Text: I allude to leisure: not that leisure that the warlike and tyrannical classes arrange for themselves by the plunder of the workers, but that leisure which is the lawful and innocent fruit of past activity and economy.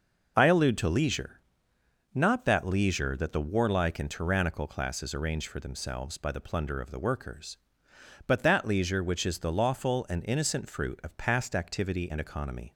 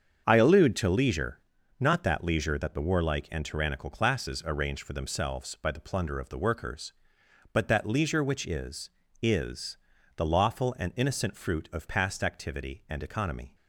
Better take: first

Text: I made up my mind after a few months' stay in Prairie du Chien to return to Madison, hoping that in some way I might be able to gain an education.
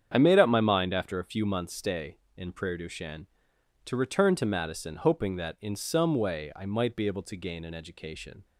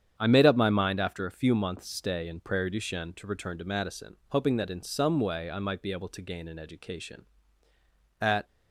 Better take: first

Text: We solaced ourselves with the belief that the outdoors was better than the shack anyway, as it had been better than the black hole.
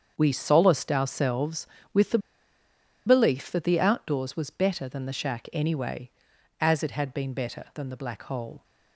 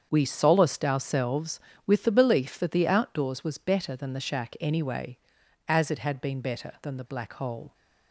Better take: second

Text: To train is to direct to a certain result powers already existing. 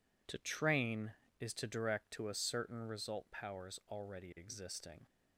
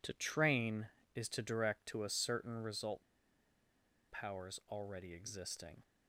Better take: first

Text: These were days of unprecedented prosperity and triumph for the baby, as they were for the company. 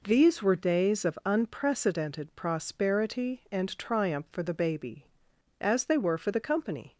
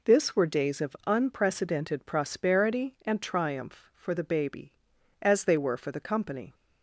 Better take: first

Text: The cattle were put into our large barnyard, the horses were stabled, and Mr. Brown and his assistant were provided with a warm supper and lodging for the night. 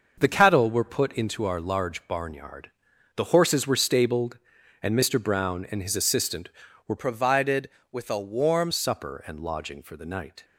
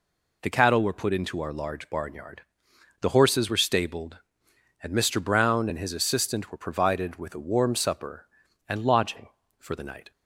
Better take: second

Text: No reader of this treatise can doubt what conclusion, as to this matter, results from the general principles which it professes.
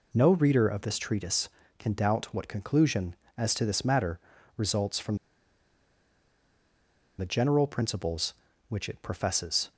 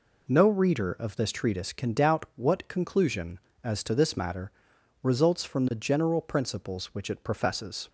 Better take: second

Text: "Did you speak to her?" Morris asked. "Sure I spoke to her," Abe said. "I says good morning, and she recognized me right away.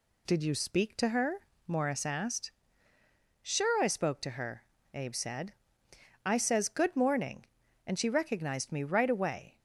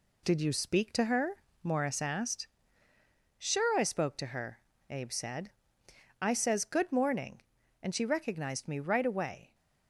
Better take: first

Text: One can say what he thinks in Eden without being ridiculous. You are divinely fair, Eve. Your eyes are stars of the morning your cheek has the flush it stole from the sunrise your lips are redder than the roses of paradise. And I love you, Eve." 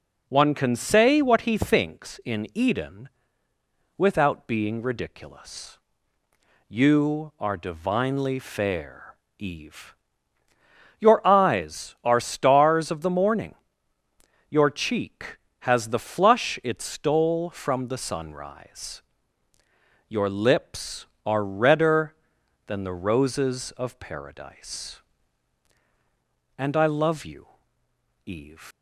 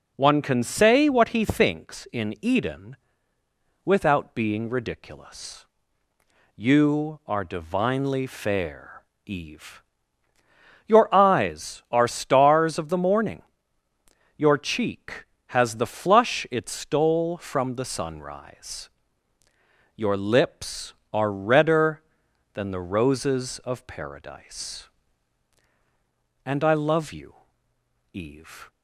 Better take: second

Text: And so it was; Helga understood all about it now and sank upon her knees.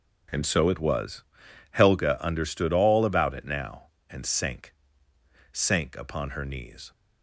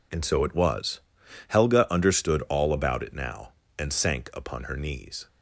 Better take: second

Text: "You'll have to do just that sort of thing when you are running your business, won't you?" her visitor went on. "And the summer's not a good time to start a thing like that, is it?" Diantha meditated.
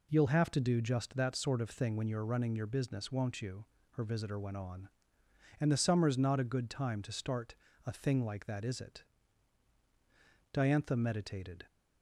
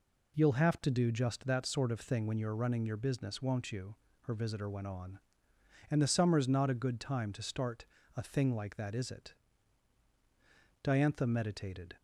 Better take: neither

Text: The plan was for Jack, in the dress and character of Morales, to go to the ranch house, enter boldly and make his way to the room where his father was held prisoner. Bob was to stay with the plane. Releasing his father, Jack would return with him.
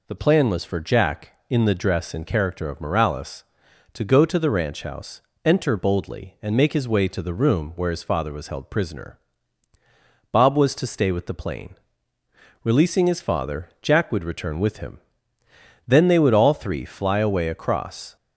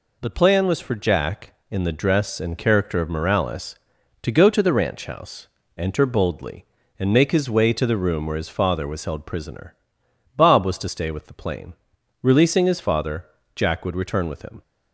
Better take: second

